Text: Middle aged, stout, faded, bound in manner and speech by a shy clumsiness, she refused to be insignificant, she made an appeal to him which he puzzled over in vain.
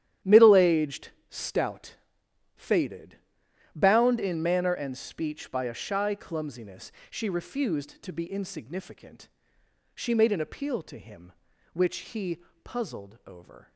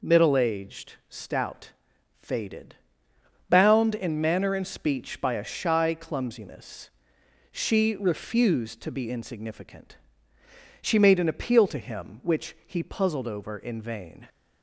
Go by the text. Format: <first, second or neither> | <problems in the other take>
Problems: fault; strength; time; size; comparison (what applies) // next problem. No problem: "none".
second | starts louder than the rest; strong; until 1.4 s; 11 dB // pauses between "he" and "puzzled"; slight; at 12.3 s; 0.28 s long // stops before "in vain"; at 13.7 s